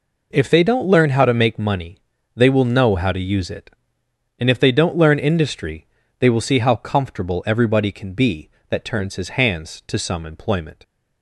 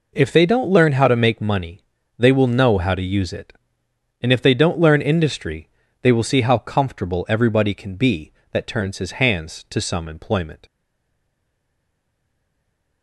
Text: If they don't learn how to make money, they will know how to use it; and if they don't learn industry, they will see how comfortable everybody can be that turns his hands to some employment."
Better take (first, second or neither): first